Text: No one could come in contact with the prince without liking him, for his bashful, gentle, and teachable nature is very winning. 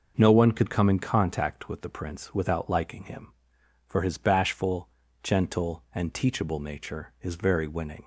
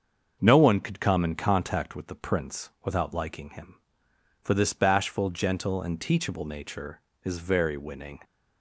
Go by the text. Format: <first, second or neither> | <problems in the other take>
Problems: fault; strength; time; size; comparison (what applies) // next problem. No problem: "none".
first | starts louder than the rest; until 1.4 s; 6.5 dB // says "this" for "his"; at 4.5 s